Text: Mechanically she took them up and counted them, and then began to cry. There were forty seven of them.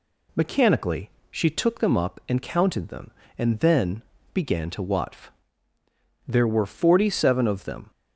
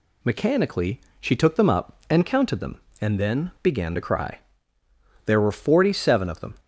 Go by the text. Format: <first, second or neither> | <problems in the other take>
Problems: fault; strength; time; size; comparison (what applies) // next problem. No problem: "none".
second | pauses between "Mechanically" and "she"; slight; at 1.1 s; 0.20 s long; slight in the second // pauses between "then" and "began"; slight; at 4.0 s; 0.32 s long // says "watf" for "cry"; at 4.8 s